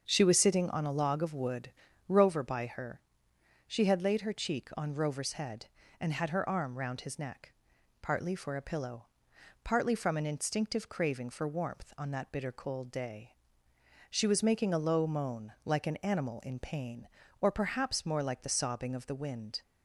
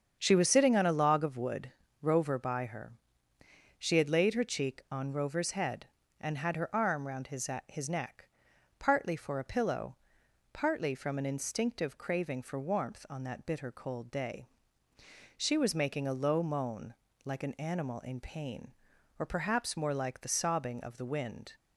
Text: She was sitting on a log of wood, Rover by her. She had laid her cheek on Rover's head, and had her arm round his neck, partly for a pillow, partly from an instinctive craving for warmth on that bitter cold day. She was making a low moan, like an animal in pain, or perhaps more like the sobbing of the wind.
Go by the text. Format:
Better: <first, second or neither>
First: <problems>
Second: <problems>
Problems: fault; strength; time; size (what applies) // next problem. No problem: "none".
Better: first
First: starts louder than the rest; until 1.0 s; 6.5 dB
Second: starts louder than the rest; strong; until 1.2 s; 7.5 dB // says "his" twice; at 7.6 s